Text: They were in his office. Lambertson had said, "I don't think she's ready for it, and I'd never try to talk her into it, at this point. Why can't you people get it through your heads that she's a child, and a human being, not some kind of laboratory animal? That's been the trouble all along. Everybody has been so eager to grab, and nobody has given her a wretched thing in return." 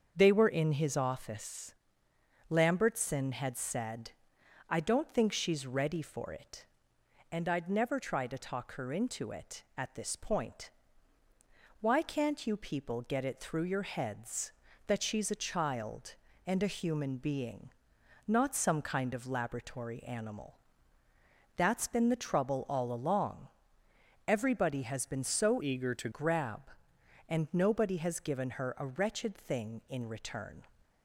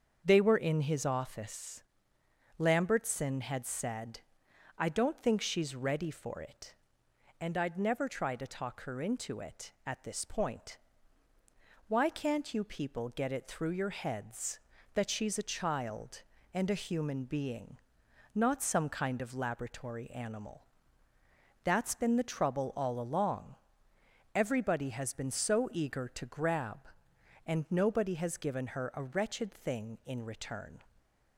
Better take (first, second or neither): second